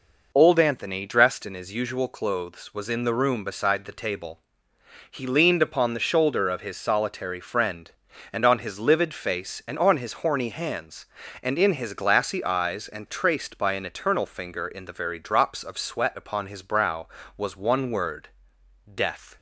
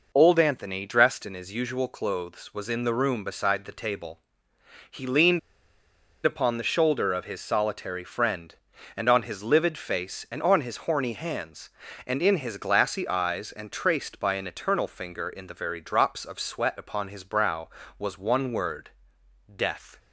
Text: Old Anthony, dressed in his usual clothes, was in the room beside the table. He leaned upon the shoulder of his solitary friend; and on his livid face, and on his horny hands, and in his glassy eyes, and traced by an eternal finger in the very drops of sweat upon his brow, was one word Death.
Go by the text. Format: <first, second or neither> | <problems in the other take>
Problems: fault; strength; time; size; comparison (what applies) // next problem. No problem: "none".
first | pauses between "leaned" and "upon"; noticeable; at 5.3 s; 0.84 s long // pauses between "word" and "Death"; noticeable; at 18.8 s; 0.66 s long; noticeable in the first